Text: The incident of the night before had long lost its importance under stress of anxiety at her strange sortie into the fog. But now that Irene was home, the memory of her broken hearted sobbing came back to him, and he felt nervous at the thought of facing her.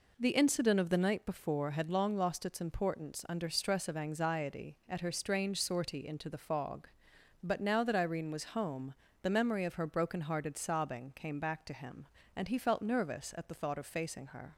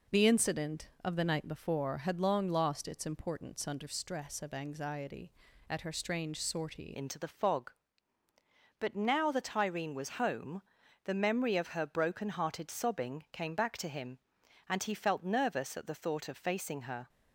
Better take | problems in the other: first | changes voice at "into"; from 6.9 s on; 10.1 s long

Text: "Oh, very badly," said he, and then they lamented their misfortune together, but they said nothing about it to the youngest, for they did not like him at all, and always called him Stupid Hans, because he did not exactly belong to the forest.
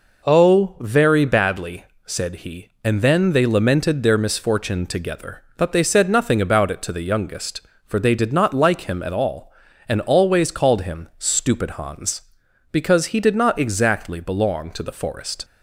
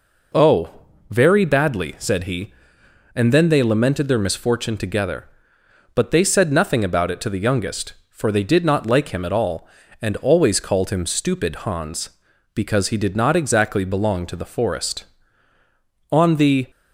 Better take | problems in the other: first | goes on to say "On the"; from 16.1 s on; 0.56 s long

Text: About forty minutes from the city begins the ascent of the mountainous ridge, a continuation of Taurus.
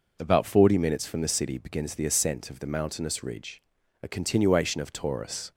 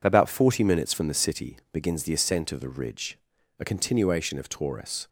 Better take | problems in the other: first | skips "mountainous"; at 2.6 s

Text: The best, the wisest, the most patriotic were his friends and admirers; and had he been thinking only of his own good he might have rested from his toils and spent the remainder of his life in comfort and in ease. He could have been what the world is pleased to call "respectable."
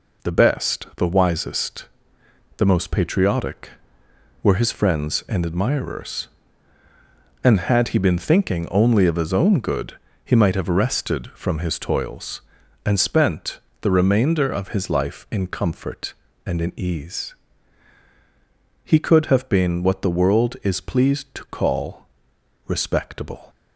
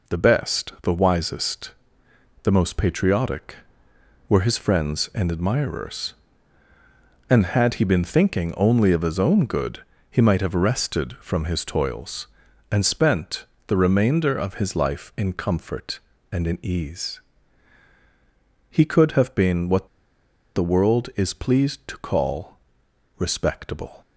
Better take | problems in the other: first | pauses between "good" and "he"; slight; at 9.8 s; 0.28 s long; slight in the first // pauses between "spent" and "the"; slight; at 13.4 s; 0.20 s long; slight in the first // pauses between "what" and "the"; noticeable; at 19.8 s; 0.67 s long // pauses between "call" and "respectable"; noticeable; at 22.5 s; 0.62 s long; noticeable in the first

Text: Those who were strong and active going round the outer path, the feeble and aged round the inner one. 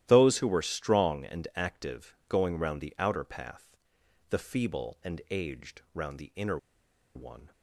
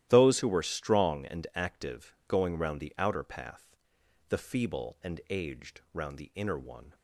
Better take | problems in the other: second | starts louder than the rest; strong; until 1.0 s; 13 dB; strong in the second // pauses between "inner" and "one"; noticeable; at 6.5 s; 0.57 s long

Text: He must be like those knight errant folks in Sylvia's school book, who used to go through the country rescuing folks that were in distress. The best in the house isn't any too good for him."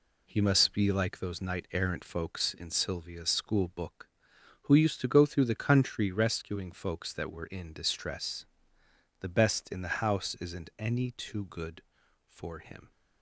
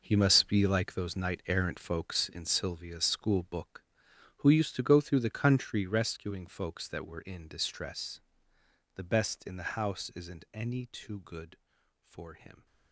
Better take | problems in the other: first | gets quieter; strong; throughout; 12.5 dB

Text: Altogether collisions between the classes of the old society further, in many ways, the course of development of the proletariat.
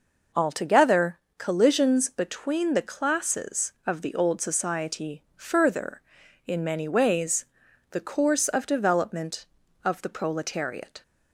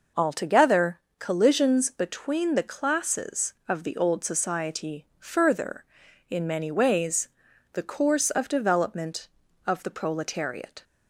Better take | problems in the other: neither | pauses between "Altogether" and "collisions"; slight; the same in both

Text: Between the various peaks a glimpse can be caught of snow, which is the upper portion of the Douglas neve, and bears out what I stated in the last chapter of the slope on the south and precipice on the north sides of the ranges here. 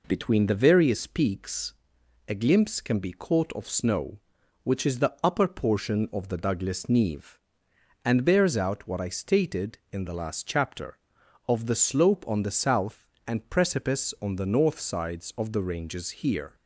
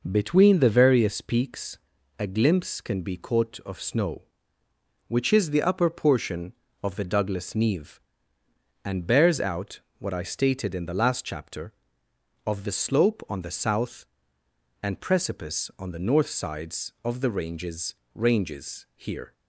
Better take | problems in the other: first | pauses between "peaks" and "a"; at 1.7 s; 0.44 s long; noticeable in the first // pauses between "out" and "what"; slight; at 9.8 s; 0.18 s long // says "ranges" twice; at 18.1 s

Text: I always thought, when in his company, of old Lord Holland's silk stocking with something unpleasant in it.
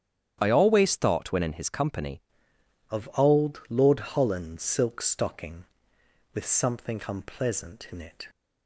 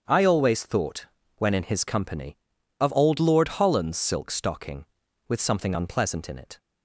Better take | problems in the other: second | starts louder than the rest; strong; until 1.4 s; 9.5 dB; strong in the second // changes voice at "of"; from 2.8 s on; 5.4 s long

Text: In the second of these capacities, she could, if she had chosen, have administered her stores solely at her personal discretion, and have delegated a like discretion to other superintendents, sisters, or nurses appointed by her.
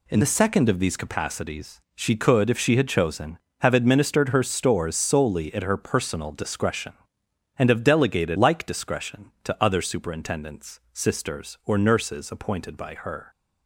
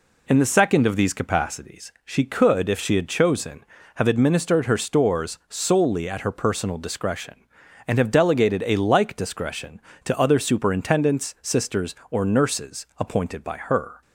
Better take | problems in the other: second | skips "a"; at 8.3 s

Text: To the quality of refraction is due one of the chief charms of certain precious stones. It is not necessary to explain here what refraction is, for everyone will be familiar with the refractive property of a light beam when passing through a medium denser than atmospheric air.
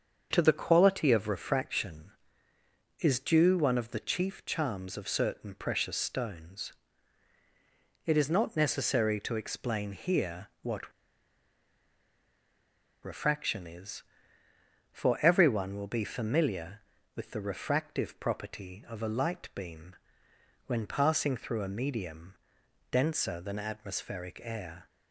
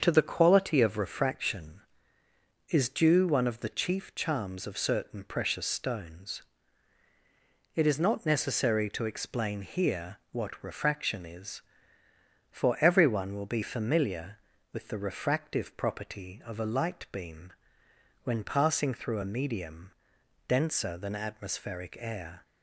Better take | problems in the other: second | starts louder than the rest; strong; until 1.3 s; 7 dB; strong in the second // pauses between "what" and "refraction"; strong; at 10.9 s; 2.1 s long // pauses between "beam" and "when"; noticeable; at 19.9 s; 0.72 s long; noticeable in the second // pauses between "medium" and "denser"; noticeable; at 22.3 s; 0.56 s long; noticeable in the second

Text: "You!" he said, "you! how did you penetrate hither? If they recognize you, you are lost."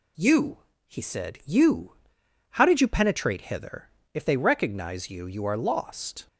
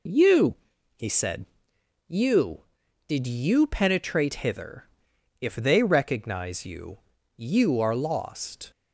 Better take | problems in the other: first | skips "how"; at 2.8 s

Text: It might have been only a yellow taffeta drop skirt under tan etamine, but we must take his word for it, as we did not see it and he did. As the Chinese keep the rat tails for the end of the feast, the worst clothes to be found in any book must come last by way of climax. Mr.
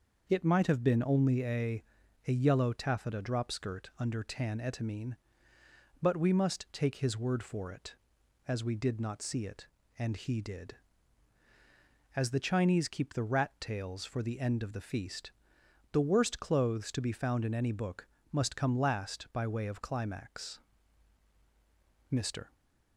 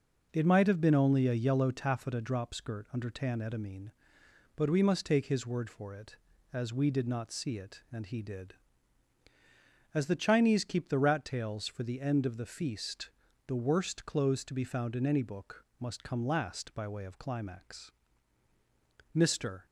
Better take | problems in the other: second | starts louder than the rest; noticeable; until 1.3 s; 6 dB // says "a" twice; at 2.2 s // pauses between "book" and "must"; slight; at 18.0 s; 0.24 s long

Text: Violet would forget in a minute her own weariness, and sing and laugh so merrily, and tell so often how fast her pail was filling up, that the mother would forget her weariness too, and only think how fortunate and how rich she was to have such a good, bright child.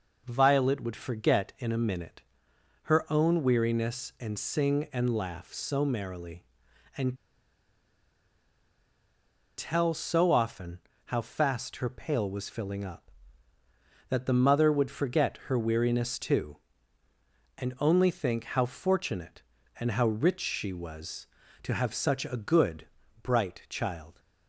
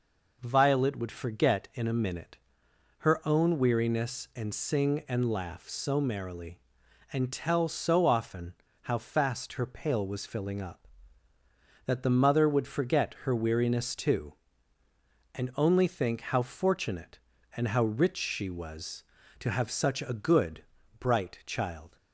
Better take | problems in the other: second | pauses between "minute" and "her"; noticeable; at 2.2 s; 0.60 s long; noticeable in the second // pauses between "and" and "tell"; strong; at 7.1 s; 2.4 s long // pauses between "often" and "how"; slight; at 10.7 s; 0.28 s long; slight in the second

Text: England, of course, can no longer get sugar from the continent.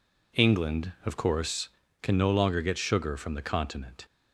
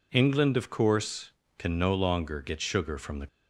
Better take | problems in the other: first | stops before "continent"; at 3.2 s

